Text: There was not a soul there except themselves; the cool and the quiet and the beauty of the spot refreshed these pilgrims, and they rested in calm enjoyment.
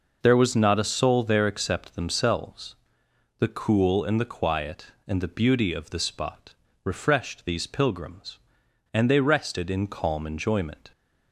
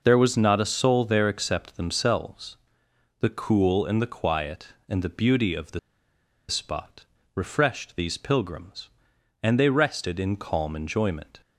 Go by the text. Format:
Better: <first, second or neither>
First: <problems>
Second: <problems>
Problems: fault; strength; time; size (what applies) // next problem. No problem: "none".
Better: first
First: pauses between "spot" and "refreshed"; slight; at 6.5 s; 0.30 s long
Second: pauses between "the" and "spot"; noticeable; at 5.7 s; 0.69 s long // pauses between "spot" and "refreshed"; slight; at 7.0 s; 0.30 s long